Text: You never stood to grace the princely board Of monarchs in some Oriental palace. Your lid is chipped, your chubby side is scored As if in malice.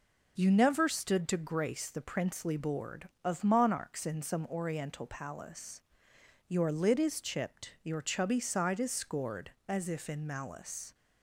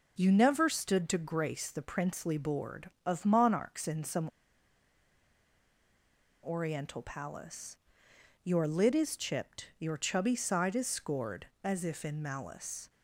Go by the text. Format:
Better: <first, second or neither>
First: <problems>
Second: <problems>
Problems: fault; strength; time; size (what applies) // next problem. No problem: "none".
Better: first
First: none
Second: pauses between "some" and "Oriental"; strong; at 4.2 s; 2.1 s long